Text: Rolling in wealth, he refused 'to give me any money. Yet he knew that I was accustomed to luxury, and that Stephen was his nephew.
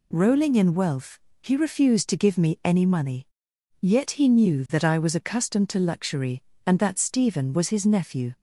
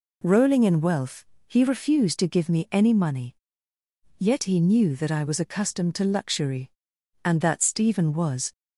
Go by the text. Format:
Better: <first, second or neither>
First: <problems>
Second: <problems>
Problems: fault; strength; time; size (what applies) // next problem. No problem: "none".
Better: first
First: none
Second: stops before "his nephew"; at 8.5 s